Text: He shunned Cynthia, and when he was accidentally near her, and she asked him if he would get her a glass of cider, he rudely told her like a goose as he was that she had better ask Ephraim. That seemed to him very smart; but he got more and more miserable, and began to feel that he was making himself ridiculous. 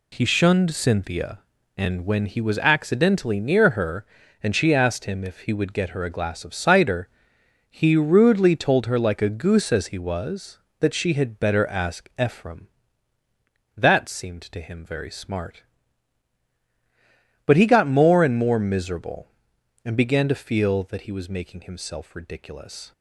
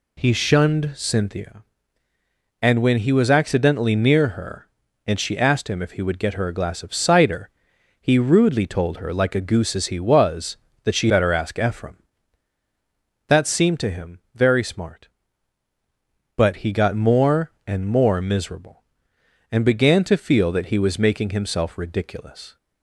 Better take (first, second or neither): first